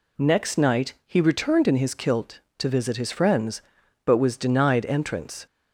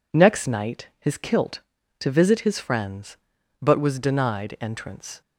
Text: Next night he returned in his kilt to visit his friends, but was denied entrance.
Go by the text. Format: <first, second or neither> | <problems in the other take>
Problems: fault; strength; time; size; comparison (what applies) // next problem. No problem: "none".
first | skips "he returned in"; at 0.9 s